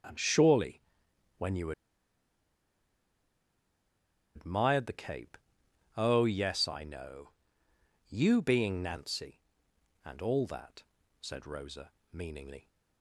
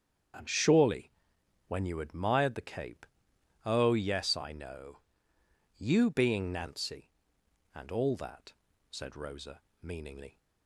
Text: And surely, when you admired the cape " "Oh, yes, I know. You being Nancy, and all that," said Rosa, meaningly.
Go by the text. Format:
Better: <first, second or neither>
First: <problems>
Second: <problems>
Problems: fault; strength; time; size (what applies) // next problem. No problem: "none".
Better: second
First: starts louder than the rest; until 1.6 s; 7 dB // pauses between "you" and "admired"; strong; at 1.7 s; 2.6 s long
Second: starts louder than the rest; until 1.9 s; 7 dB